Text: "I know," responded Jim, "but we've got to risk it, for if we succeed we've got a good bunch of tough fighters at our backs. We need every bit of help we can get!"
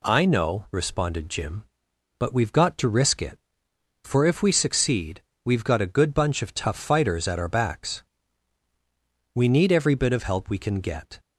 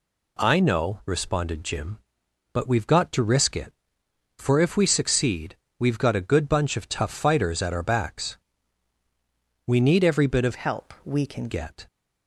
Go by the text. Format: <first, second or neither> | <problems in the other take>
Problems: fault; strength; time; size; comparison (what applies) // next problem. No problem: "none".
first | pauses between "succeed" and "we've"; slight; at 5.5 s; 0.24 s long; slight in the first // changes voice from "help" to "can"; from 10.5 to 11.4 s; 0.9 s long